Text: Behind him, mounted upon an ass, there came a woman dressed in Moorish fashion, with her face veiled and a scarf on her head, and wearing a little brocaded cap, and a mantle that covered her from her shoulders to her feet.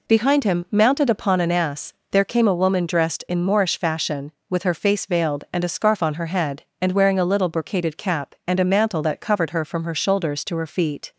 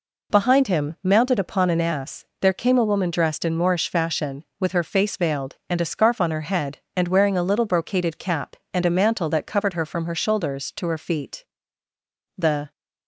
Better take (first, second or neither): first